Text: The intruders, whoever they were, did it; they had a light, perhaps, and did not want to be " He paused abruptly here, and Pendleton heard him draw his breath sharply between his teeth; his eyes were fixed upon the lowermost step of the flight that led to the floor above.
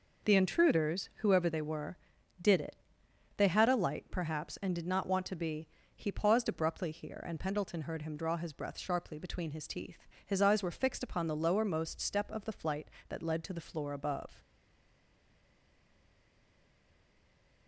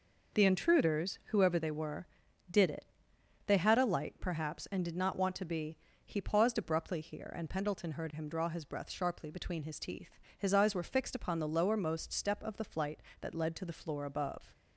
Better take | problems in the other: second | stays silent after the last word; strong; from 14.3 s on; 3.3 s long

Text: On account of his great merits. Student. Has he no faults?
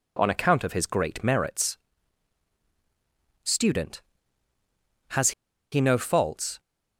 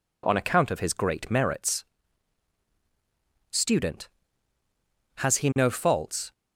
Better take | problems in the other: second | pauses between "Has" and "he"; at 5.3 s; 0.40 s long

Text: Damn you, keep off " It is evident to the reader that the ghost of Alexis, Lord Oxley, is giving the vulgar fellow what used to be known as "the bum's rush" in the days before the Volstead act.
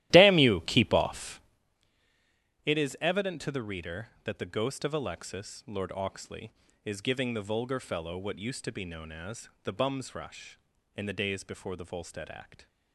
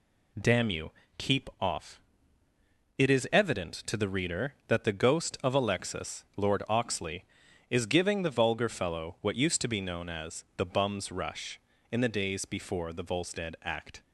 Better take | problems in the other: second | starts louder than the rest; strong; until 1.8 s; 15 dB // pauses between "as" and "the"; slight; at 9.4 s; 0.16 s long

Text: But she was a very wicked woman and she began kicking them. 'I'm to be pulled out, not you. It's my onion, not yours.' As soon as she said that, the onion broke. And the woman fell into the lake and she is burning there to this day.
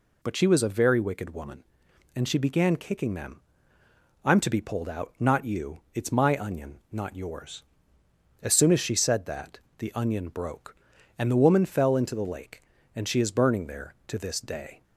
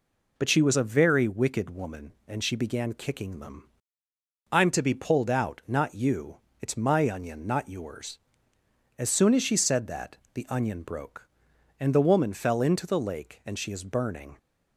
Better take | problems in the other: first | stops before "there to this day"; at 14.3 s

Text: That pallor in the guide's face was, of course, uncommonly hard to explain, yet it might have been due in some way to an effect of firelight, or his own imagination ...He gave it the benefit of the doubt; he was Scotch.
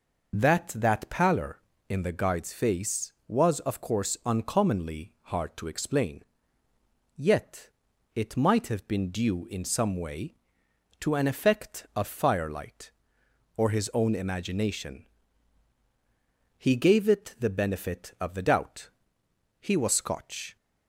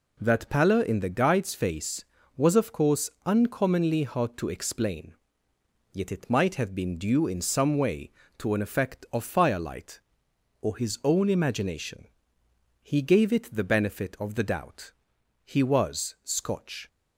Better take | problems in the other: second | says "That" twice; at 0.7 s // pauses between "uncommonly" and "hard"; slight; at 5.1 s; 0.18 s long // pauses between "yet" and "it"; noticeable; at 7.6 s; 0.48 s long

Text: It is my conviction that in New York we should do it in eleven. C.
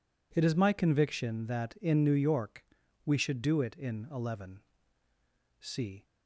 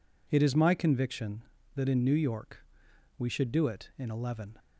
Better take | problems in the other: first | pauses between "York" and "we"; noticeable; at 2.5 s; 0.60 s long; also in the first // stops before "C"; at 4.5 s

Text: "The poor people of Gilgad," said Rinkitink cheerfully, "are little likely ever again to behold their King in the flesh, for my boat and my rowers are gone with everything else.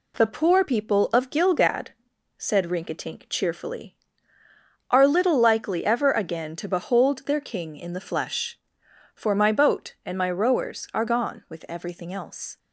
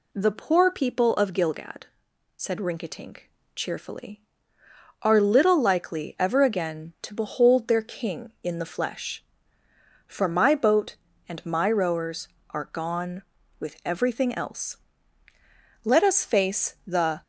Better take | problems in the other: first | pauses between "Rinkitink" and "cheerfully"; slight; at 3.3 s; 0.24 s long // goes on to say "Let us face the"; from 15.8 s on; 1.3 s long

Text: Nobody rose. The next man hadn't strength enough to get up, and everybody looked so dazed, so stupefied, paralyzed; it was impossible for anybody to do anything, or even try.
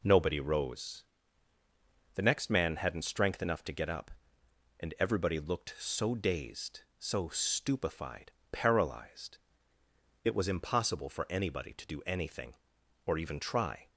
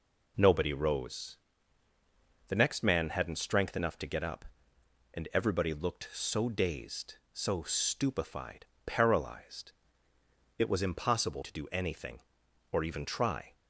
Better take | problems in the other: first | skips "for anybody"; at 11.4 s

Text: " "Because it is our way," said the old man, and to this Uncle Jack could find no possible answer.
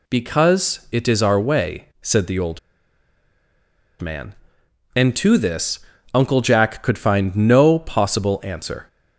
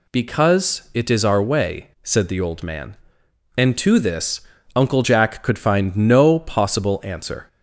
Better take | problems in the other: second | pauses between "old" and "man"; strong; at 2.5 s; 1.4 s long // pauses between "this" and "Uncle"; slight; at 5.7 s; 0.34 s long; slight in the second

